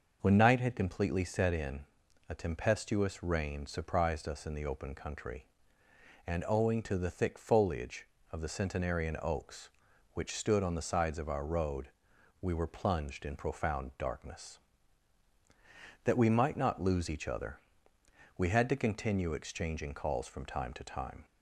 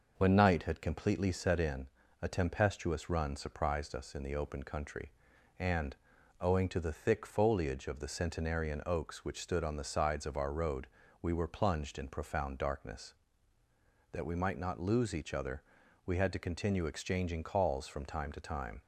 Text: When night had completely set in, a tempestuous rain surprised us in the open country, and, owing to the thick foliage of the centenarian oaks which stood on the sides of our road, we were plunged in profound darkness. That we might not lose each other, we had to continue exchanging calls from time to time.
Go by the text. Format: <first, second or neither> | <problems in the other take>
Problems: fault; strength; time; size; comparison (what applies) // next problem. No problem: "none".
first | starts louder than the rest; noticeable; until 1.1 s; 6 dB; noticeable in the first // says "run" for "rain"; at 3.1 s